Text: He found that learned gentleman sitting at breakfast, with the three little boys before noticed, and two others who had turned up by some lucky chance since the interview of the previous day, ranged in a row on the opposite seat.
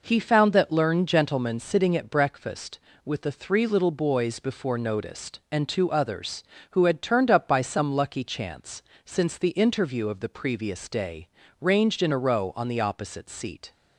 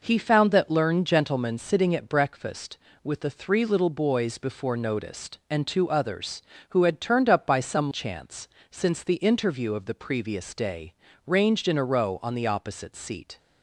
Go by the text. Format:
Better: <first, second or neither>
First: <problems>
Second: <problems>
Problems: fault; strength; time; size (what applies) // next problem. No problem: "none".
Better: first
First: pauses between "chance" and "since"; slight; at 8.8 s; 0.24 s long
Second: skips "lucky"; at 7.9 s // pauses between "chance" and "since"; slight; at 8.4 s; 0.24 s long